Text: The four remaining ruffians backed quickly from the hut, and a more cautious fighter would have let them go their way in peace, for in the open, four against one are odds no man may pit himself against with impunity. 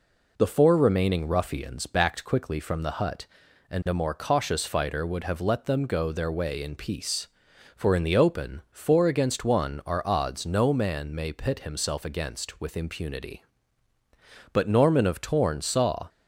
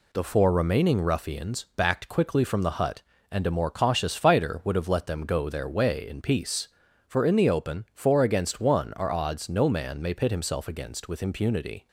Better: second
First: goes on to say "But Norman of Torn saw"; from 14.5 s on; 1.5 s long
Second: none

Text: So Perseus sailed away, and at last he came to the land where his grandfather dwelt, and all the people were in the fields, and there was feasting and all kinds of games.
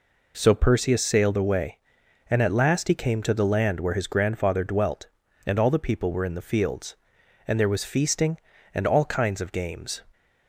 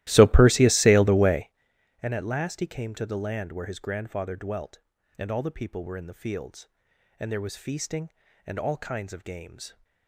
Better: first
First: none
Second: starts louder than the rest; strong; until 1.7 s; 15.5 dB

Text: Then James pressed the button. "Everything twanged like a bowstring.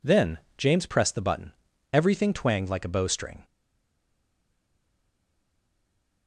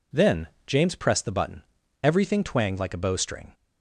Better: second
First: pauses between "Then" and "James"; slight; at 0.3 s; 0.20 s long // stays silent after the last word; strong; from 3.4 s on; 2.8 s long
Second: pauses between "Then" and "James"; slight; at 0.4 s; 0.20 s long

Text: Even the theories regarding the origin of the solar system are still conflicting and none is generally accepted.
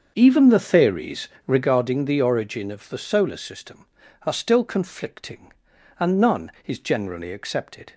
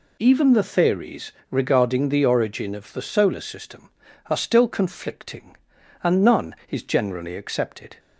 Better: second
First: starts louder than the rest; until 1.7 s; 6.5 dB // pauses between "theories" and "regarding"; slight; at 1.2 s; 0.16 s long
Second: pauses between "theories" and "regarding"; slight; at 1.3 s; 0.16 s long

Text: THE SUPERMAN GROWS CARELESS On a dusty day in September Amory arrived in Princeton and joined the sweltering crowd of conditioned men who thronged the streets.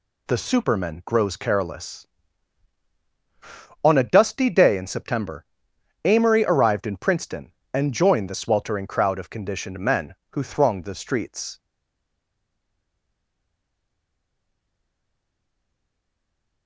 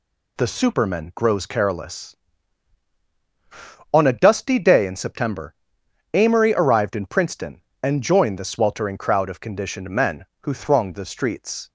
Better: second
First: pauses between "September" and "Amory"; noticeable; at 5.4 s; 0.58 s long // stays silent after the last word; strong; from 11.5 s on; 5.1 s long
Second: pauses between "September" and "Amory"; noticeable; at 5.5 s; 0.58 s long

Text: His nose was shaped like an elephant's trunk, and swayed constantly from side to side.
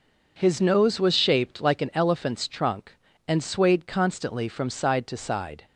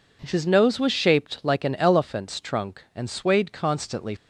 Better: first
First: none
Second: stops before "from side to side"; at 4.1 s

